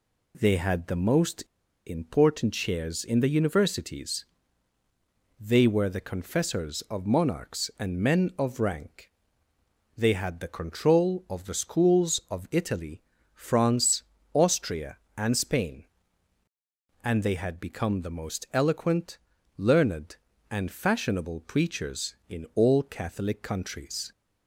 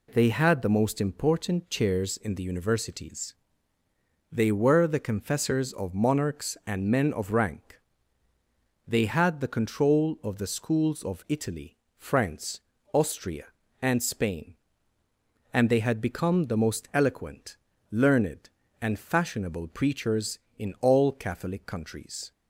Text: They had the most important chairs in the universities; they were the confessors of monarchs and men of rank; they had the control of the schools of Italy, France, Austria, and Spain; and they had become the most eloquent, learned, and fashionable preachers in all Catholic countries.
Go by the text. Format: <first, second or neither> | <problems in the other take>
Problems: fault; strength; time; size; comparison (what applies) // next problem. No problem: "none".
second | pauses between "most" and "important"; at 1.4 s; 0.44 s long